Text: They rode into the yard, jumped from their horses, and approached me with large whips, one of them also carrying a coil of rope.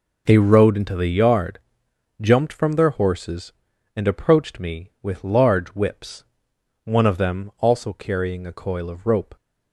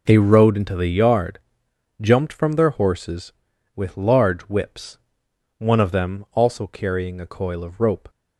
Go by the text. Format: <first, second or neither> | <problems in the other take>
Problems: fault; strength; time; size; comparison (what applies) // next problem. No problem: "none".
first | skips "and approached me"; at 3.5 s